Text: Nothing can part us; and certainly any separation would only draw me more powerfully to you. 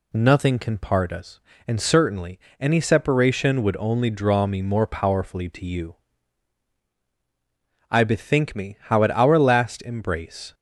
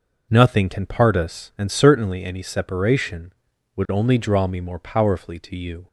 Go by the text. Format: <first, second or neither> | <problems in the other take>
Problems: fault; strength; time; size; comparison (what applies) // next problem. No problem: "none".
second | pauses between "certainly" and "any"; slight; at 2.3 s; 0.22 s long // goes on to say "I bethink me how at our last embrace"; strong; from 7.8 s on; 2.6 s long